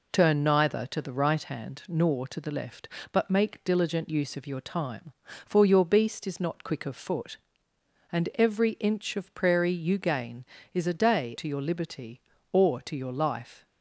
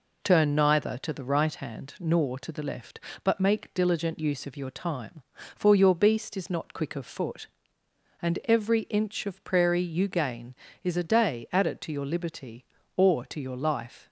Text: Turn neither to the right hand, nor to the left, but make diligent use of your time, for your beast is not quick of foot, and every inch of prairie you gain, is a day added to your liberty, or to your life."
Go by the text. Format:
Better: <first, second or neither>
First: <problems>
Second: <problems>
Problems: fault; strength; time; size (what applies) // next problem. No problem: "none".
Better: second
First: skips "added"; at 11.3 s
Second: none